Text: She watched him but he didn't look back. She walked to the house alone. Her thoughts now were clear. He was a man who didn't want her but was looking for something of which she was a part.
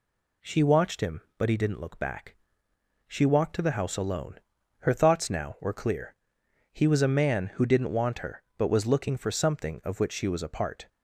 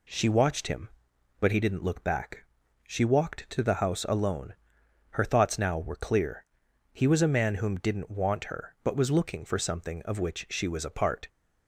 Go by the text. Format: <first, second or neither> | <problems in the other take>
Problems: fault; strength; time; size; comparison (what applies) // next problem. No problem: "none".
first | says "whom" for "who"; at 7.5 s